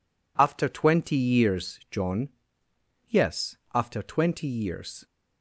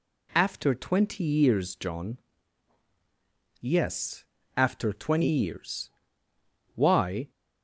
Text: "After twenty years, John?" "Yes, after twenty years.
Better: first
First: none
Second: goes on to say "Why"; from 6.7 s on; 0.56 s long

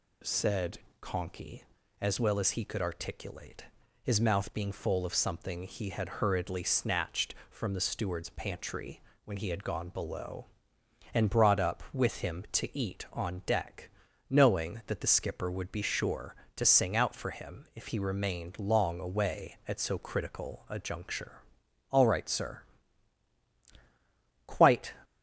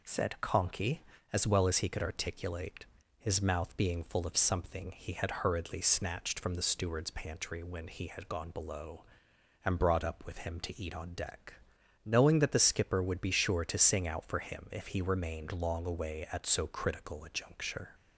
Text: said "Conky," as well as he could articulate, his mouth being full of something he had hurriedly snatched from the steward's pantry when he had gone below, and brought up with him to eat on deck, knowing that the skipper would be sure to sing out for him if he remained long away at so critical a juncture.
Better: second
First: pauses between "said" and "Conky"; slight; at 0.7 s; 0.22 s long // pauses between "pantry" and "when"; slight; at 9.0 s; 0.24 s long // goes on to say "All right sir quite"; strong; from 21.9 s on; 3.0 s long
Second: none

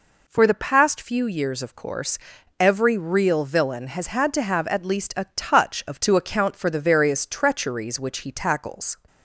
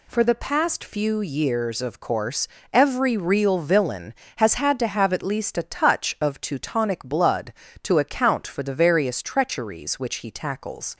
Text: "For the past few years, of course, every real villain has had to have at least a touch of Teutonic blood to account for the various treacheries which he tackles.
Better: second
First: skips "Teutonic blood"; at 6.0 s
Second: none

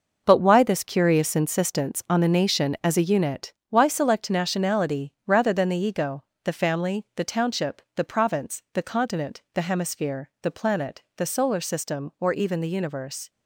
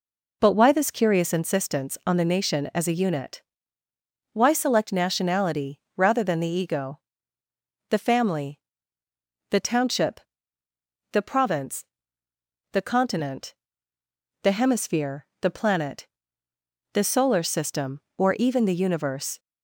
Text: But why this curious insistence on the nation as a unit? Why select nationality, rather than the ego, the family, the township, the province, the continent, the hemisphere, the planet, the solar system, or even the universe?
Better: second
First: gets quieter; strong; throughout; 9.5 dB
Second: none

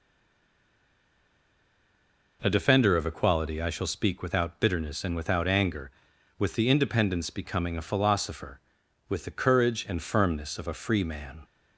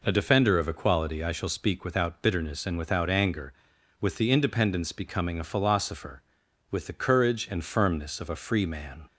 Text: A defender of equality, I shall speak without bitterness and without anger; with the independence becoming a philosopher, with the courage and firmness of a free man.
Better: second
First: stays silent before the first word; until 2.4 s; 2.4 s long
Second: none

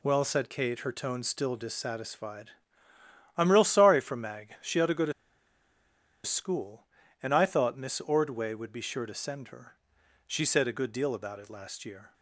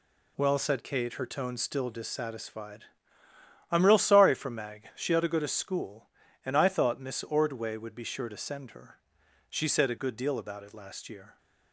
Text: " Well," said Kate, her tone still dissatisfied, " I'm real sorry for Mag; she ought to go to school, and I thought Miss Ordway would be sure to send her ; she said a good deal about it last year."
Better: second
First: pauses between "to" and "school"; at 5.1 s; 1.1 s long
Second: none

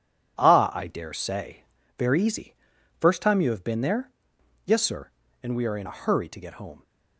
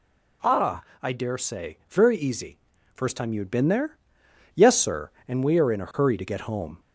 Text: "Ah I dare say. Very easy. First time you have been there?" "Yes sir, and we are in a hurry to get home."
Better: first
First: none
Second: pauses between "Ah" and "I"; slight; at 0.8 s; 0.18 s long // says "had" for "have"; at 3.4 s

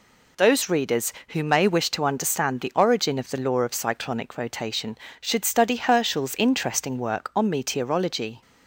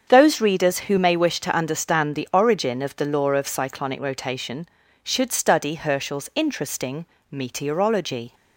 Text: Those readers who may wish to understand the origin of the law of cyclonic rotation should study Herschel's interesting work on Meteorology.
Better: first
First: none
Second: starts louder than the rest; strong; until 1.1 s; 7 dB // skips "work on"; at 7.1 s

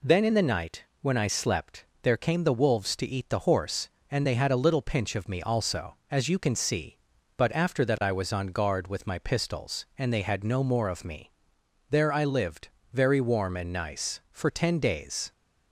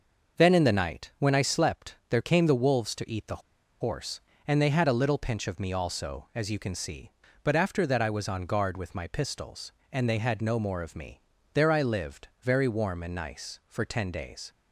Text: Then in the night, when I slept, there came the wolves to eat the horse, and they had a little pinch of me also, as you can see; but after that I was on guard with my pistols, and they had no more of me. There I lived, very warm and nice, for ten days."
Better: first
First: none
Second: pauses between "the" and "horse"; at 3.4 s; 0.39 s long

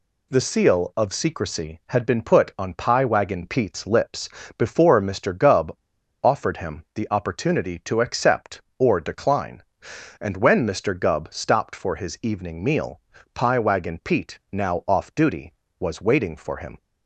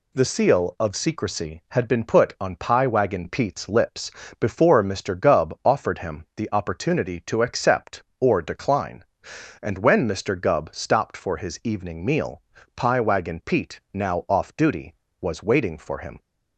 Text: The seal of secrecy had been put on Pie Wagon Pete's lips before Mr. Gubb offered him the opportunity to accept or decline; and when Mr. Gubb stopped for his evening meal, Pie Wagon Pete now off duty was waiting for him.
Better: second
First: pauses between "lips" and "before"; slight; at 4.2 s; 0.30 s long // pauses between "Gubb" and "offered"; noticeable; at 5.7 s; 0.48 s long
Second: pauses between "lips" and "before"; slight; at 4.1 s; 0.30 s long

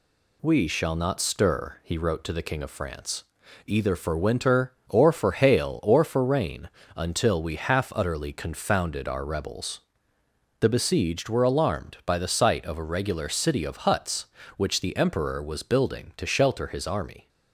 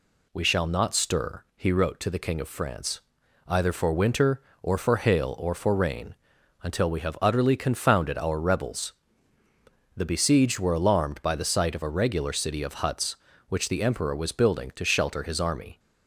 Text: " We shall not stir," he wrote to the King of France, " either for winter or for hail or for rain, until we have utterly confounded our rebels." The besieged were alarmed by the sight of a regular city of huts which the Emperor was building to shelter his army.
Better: second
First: says "half" for "have"; at 7.5 s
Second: none

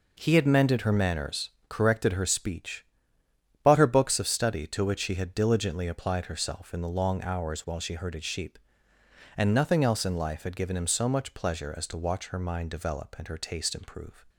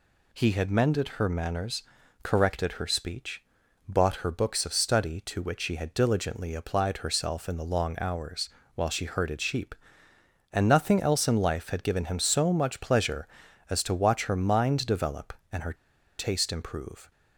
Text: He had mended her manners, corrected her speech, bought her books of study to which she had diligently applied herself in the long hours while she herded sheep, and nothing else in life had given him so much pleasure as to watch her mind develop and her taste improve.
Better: first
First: none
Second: pauses between "hours" and "while"; slight; at 8.4 s; 0.26 s long // pauses between "her" and "taste"; at 15.7 s; 0.43 s long

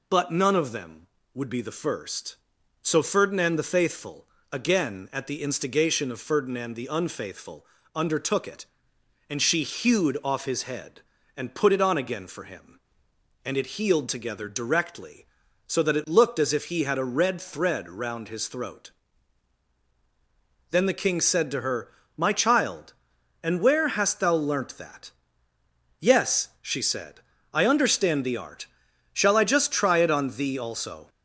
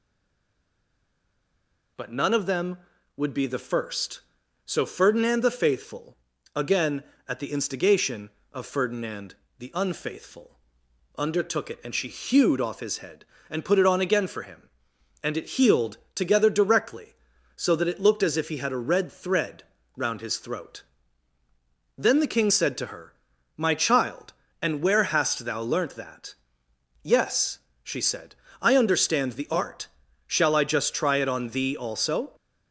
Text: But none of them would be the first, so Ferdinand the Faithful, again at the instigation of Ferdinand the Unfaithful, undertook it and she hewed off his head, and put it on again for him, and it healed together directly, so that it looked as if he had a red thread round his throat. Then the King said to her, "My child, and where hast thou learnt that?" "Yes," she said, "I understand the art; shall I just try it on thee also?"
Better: first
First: none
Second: stays silent before the first word; noticeable; until 1.9 s; 1.9 s long // pauses between "Ferdinand" and "the"; slight; at 9.3 s; 0.24 s long // pauses between "healed" and "together"; slight; at 15.9 s; 0.18 s long // pauses between "thread" and "round"; slight; at 19.6 s; 0.34 s long

